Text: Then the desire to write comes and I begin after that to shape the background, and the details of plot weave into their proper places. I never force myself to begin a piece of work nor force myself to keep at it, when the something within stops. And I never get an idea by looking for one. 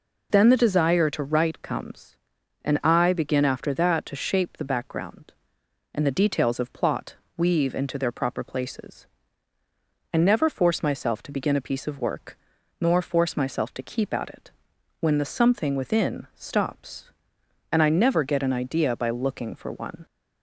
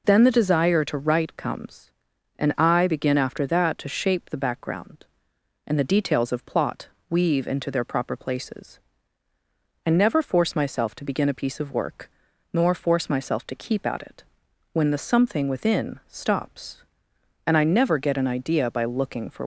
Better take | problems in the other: first | pauses between "plot" and "weave"; slight; at 6.8 s; 0.20 s long; slight in the first // pauses between "work" and "nor"; at 12.0 s; 0.42 s long; also in the first // stops before "one"; at 19.4 s

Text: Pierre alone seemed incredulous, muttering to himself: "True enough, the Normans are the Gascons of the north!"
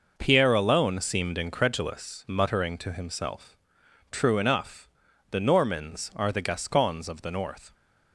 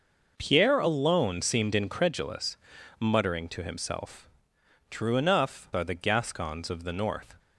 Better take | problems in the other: first | skips "the Normans"; at 5.7 s

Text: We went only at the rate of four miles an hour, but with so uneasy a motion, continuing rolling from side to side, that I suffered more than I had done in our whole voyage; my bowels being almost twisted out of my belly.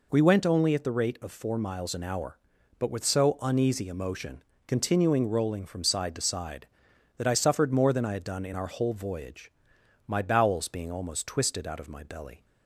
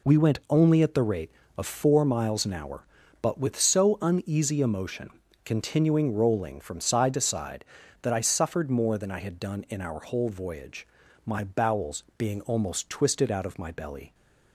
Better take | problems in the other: neither | none

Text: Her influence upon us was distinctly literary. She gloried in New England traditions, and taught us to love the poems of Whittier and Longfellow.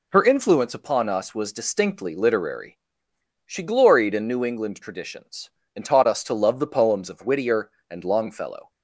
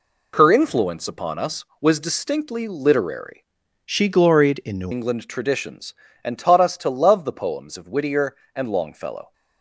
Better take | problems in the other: first | changes voice from "She" to "New"; from 3.8 to 4.9 s; 1.1 s long

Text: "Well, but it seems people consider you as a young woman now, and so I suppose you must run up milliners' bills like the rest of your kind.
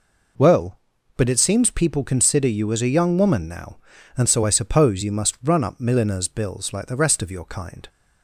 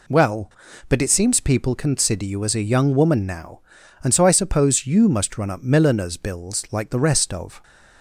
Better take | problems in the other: first | stops before "your kind"; at 7.6 s

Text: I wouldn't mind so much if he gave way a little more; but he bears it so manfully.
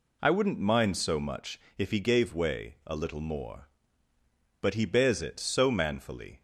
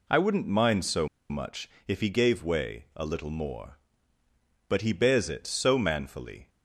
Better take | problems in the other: first | pauses between "so" and "much"; slight; at 1.0 s; 0.22 s long // pauses between "much" and "if"; slight; at 1.6 s; 0.18 s long; slight in the first

